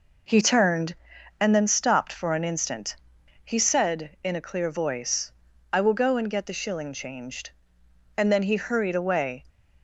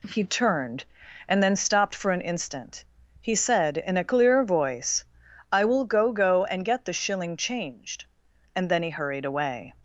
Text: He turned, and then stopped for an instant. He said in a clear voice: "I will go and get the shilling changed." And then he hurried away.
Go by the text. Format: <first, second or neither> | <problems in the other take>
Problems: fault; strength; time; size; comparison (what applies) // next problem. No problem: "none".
first | says "go" twice; at 6.1 s